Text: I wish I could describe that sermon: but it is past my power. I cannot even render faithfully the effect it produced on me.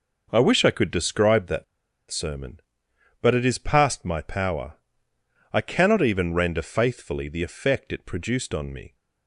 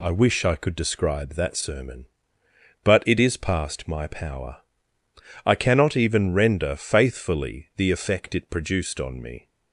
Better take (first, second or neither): second